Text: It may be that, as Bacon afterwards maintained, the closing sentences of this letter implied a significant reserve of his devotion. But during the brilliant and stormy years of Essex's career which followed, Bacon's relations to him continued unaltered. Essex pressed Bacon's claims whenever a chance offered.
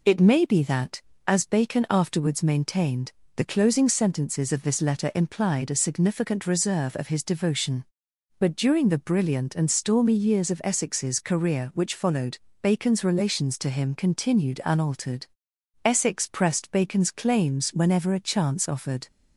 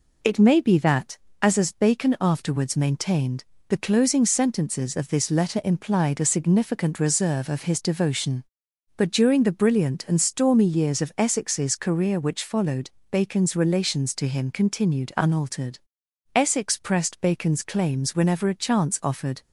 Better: first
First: none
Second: says "as" twice; at 1.5 s

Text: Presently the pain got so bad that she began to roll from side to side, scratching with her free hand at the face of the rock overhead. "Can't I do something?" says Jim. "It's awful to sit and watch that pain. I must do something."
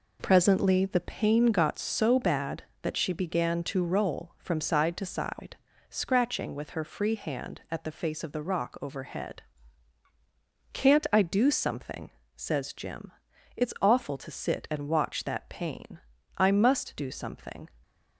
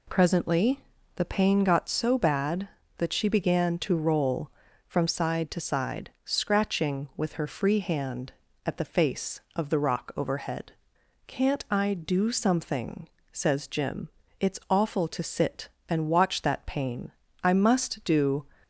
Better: first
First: none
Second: pauses between "Presently" and "the"; slight; at 0.8 s; 0.36 s long // stops before "something"; at 18.6 s

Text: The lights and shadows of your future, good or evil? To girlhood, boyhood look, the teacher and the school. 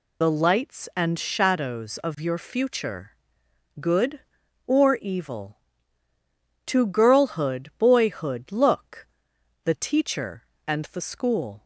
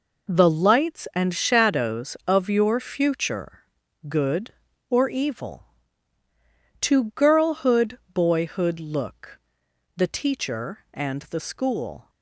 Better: second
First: loses the start of "The"; at 0.2 s; 75 ms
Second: none

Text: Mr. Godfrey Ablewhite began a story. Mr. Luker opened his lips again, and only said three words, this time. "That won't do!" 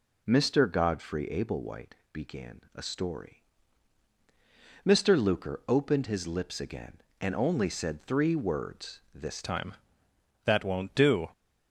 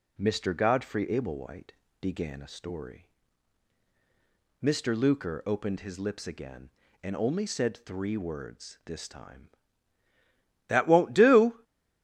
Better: second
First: pauses between "Ablewhite" and "began"; slight; at 1.9 s; 0.18 s long // changes voice at "time"; from 9.4 s on; 1.8 s long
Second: pauses between "Ablewhite" and "began"; slight; at 1.7 s; 0.28 s long

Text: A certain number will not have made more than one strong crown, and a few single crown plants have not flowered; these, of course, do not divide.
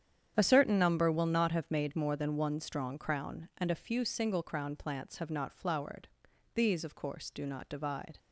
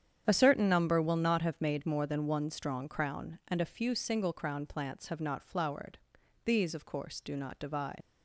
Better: first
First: starts louder than the rest; strong; until 1.3 s; 9 dB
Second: starts louder than the rest; strong; until 1.2 s; 9 dB // leaves "divide" unfinished; at 8.0 s; 75 ms

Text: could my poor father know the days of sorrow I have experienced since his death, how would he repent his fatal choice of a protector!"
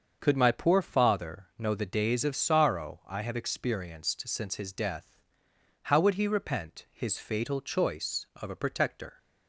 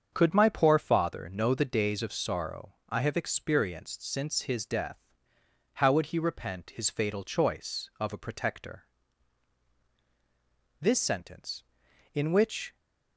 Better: first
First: starts louder than the rest; until 1.2 s; 6.5 dB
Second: starts louder than the rest; until 1.1 s; 7 dB // goes on to say "This sentence in which"; strong; from 10.7 s on; 1.9 s long

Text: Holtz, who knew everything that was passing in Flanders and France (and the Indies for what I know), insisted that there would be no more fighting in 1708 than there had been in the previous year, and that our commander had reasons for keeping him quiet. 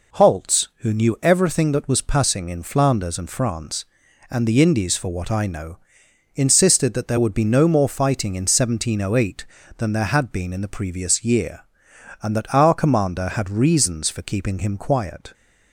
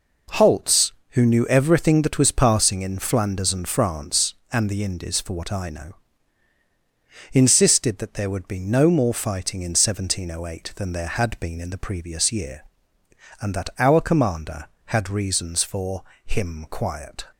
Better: first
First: none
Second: skips "keeping"; at 16.1 s

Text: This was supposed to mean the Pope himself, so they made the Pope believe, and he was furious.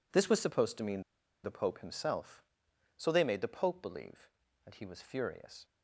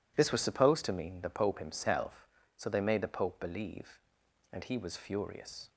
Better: second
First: pauses between "mean" and "the"; at 1.0 s; 0.41 s long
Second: none

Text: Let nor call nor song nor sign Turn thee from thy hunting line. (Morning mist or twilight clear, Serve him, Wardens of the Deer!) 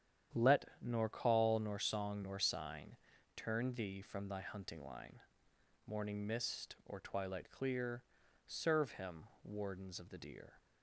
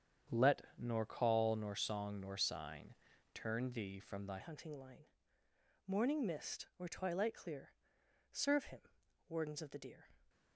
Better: first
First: starts louder than the rest; strong; until 1.5 s; 9.5 dB // pauses between "Let" and "nor"; slight; at 0.6 s; 0.18 s long // pauses between "sign" and "Turn"; at 2.9 s; 0.40 s long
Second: starts louder than the rest; strong; until 1.4 s; 8 dB // pauses between "Let" and "nor"; slight; at 0.6 s; 0.18 s long // pauses between "sign" and "Turn"; at 2.9 s; 0.40 s long // changes voice at "hunting"; from 4.3 s on; 5.7 s long

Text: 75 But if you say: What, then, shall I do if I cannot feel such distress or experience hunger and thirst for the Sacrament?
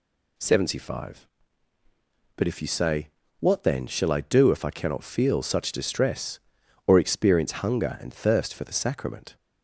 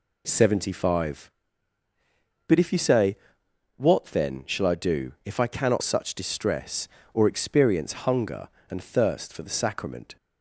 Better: first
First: none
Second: skips "feel"; at 5.8 s

